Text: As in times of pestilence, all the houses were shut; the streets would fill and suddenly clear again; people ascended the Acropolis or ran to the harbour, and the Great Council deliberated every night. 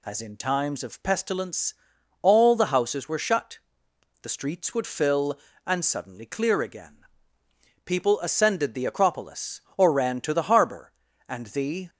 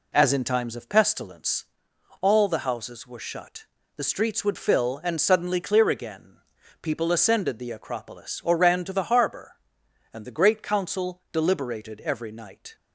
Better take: second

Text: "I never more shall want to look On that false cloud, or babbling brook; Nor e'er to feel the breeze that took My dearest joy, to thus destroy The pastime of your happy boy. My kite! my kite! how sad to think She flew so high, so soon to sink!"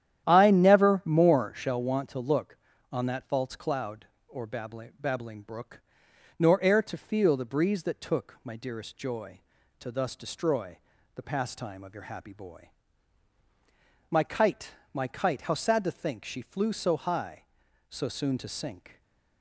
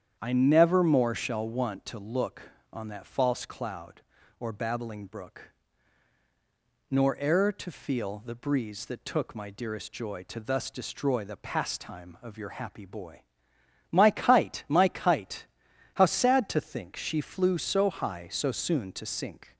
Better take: second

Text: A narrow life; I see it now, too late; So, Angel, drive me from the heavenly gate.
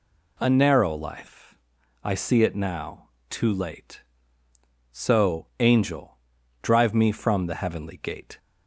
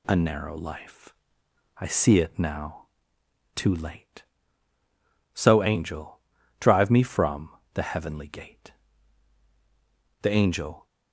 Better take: first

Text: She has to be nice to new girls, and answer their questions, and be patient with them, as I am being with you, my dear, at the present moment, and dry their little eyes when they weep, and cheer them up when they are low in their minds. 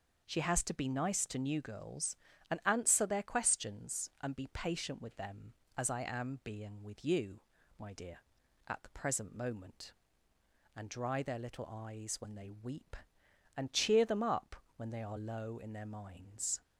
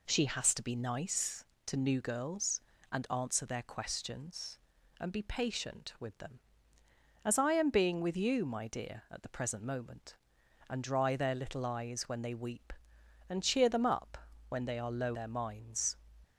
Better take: first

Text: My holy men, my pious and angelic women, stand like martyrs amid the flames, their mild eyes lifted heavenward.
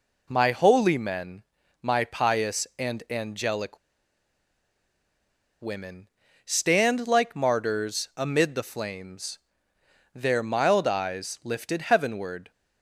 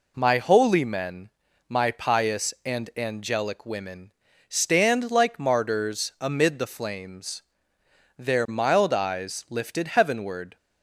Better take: second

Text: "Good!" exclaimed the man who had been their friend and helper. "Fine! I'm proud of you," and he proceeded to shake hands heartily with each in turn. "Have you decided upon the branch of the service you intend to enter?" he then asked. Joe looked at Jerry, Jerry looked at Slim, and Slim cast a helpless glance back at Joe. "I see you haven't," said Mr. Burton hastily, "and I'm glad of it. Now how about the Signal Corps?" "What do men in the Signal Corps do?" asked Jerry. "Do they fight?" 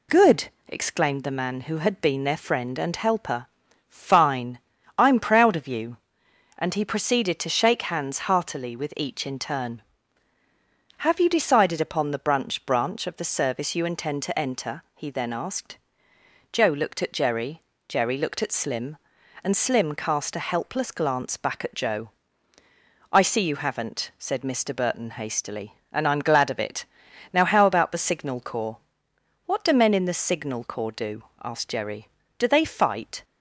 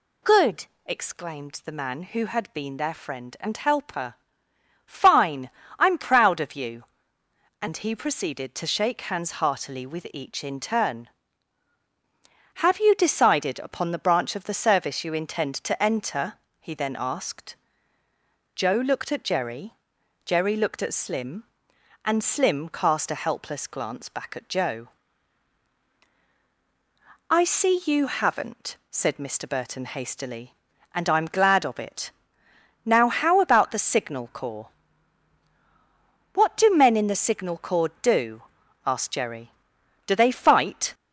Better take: second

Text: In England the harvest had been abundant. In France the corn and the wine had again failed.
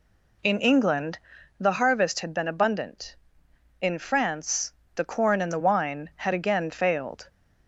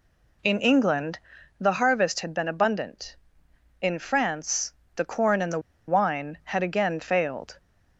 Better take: first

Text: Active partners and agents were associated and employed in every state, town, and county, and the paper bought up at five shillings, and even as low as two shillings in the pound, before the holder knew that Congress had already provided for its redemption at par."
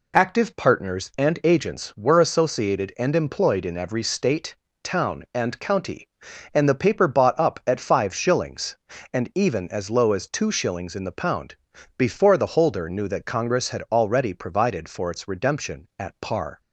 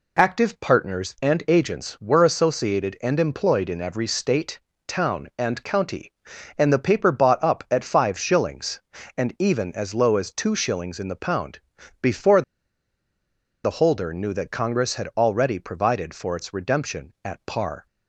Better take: first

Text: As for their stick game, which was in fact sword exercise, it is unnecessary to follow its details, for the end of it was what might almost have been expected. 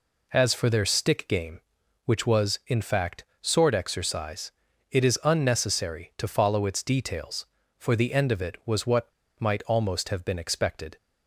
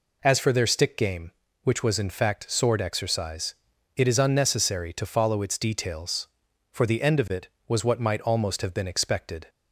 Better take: second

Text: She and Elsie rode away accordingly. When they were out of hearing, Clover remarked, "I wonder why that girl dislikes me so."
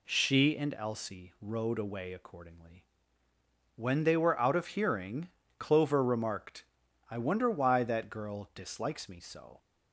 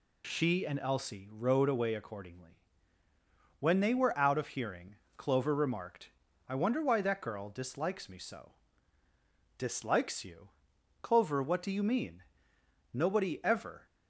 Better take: first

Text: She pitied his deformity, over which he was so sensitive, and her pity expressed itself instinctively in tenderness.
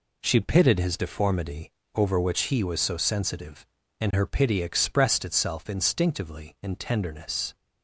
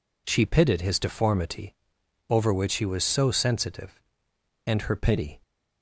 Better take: first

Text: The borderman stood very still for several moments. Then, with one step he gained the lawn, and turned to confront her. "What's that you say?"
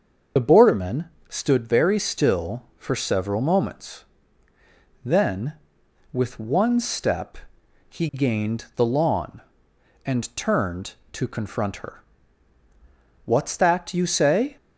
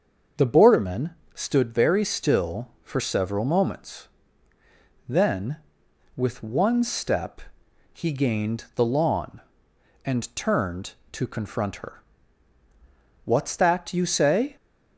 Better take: second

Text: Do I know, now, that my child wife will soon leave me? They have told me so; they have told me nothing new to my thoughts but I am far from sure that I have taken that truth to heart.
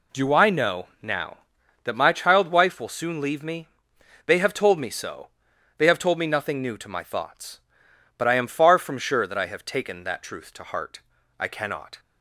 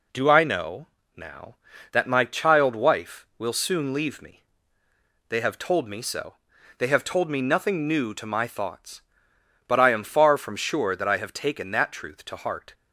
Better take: second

